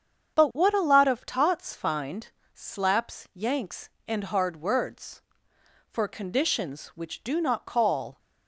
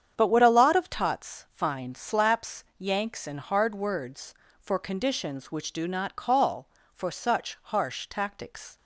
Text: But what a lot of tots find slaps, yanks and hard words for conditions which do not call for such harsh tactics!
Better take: second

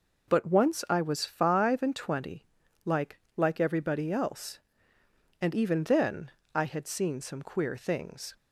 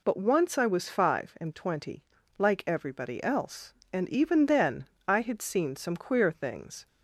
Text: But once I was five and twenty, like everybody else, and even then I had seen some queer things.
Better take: second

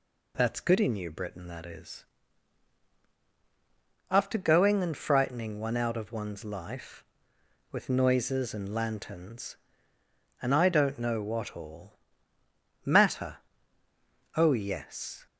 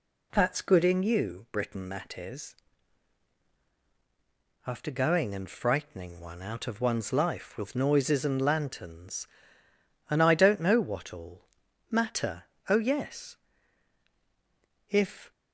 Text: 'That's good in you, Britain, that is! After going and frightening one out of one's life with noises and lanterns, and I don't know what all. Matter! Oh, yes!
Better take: first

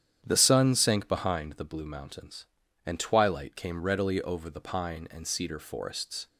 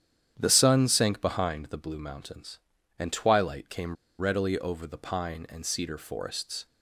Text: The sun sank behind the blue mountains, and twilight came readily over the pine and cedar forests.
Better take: first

